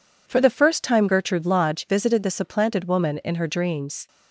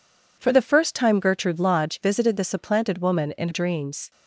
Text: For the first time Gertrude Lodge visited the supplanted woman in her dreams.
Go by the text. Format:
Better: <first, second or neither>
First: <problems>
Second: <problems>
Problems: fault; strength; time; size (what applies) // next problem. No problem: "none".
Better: first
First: none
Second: skips "her"; at 3.4 s